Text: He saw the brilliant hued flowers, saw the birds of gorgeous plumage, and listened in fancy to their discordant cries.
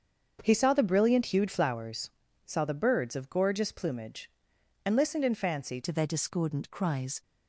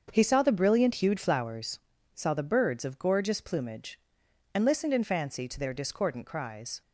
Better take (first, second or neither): second